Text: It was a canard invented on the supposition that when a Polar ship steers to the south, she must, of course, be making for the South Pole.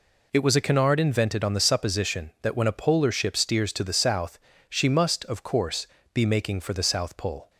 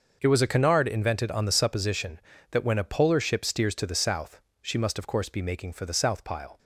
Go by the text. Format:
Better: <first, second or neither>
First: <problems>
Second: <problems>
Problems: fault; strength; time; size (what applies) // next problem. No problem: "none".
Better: first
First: none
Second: starts louder than the rest; until 1.2 s; 6 dB // says "Pile" for "Pole"; at 6.2 s